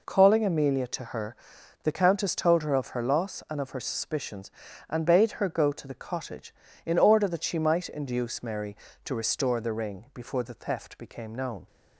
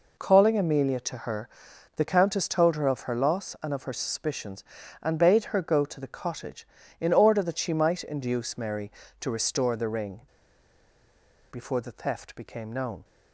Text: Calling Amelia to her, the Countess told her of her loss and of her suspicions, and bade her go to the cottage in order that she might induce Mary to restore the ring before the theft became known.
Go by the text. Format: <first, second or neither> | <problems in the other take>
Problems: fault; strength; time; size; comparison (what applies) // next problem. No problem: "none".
first | pauses between "ring" and "before"; strong; at 10.2 s; 1.2 s long